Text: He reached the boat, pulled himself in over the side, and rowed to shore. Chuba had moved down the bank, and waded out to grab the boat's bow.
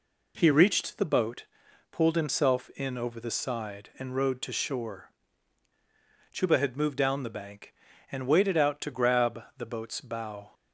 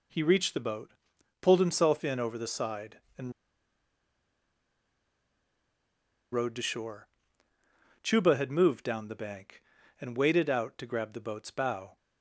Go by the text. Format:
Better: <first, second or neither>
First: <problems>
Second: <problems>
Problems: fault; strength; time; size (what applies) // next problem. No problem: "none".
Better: first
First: none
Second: pauses between "and" and "rowed"; strong; at 3.3 s; 3.0 s long